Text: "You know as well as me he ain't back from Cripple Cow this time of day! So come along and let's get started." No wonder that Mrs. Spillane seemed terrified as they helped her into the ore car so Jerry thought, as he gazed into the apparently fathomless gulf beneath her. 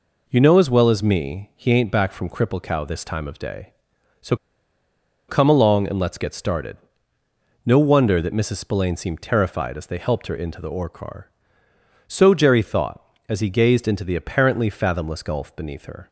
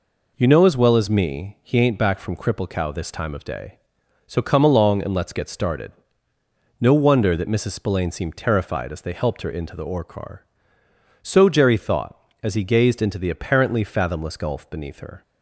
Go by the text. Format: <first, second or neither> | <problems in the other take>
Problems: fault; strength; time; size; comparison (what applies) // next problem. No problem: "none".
second | pauses between "So" and "come"; noticeable; at 4.3 s; 0.93 s long